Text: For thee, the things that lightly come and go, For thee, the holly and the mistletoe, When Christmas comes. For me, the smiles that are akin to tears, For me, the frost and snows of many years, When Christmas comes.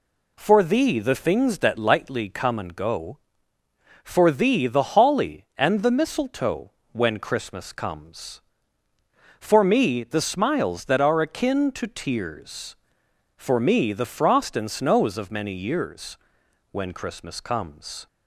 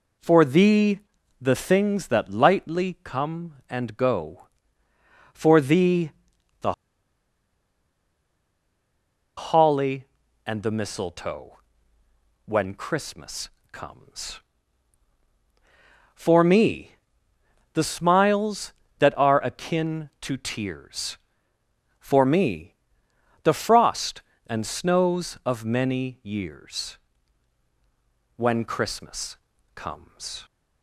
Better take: first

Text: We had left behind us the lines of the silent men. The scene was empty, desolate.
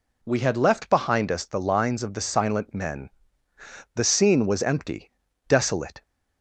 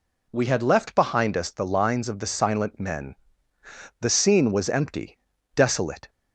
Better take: neither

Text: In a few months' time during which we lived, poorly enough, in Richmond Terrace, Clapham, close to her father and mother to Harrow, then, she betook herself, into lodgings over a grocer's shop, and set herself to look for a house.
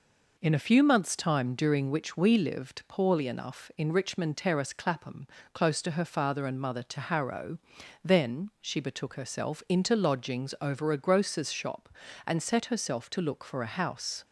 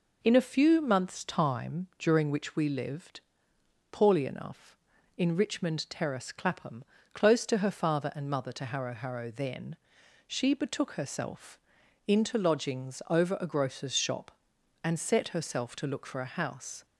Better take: first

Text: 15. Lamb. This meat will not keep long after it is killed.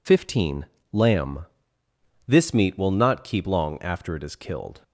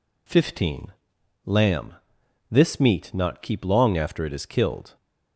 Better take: first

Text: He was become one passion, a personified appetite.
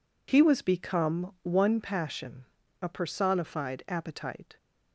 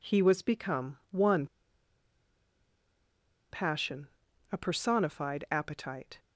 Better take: first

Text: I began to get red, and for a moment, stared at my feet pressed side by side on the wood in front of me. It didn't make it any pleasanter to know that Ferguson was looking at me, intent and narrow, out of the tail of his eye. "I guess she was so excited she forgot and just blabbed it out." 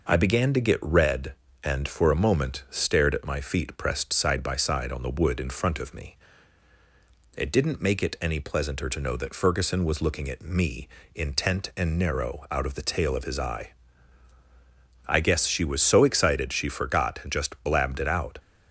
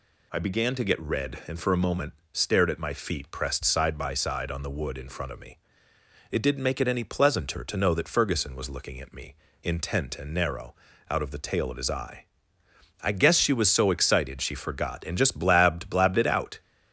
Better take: first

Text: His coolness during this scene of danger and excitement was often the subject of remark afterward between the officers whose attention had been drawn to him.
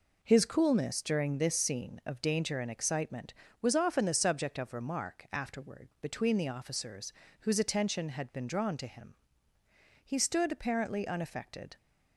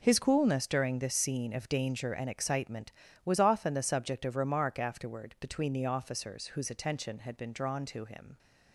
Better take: second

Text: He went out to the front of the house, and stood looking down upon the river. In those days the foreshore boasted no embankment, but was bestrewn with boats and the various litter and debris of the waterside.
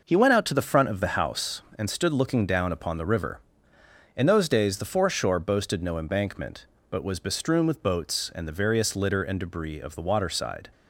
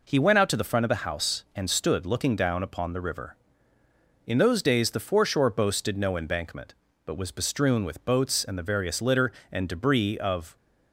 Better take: first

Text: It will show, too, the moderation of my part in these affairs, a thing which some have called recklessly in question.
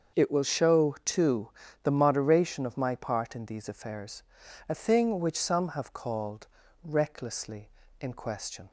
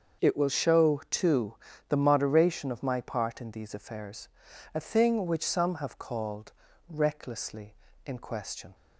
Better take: neither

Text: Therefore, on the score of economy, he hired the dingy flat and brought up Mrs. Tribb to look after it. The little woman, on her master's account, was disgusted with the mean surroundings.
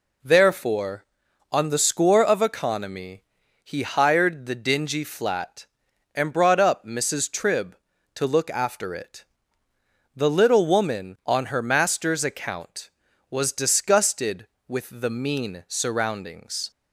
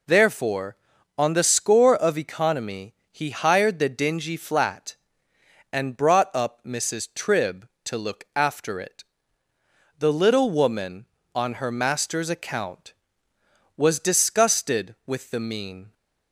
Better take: first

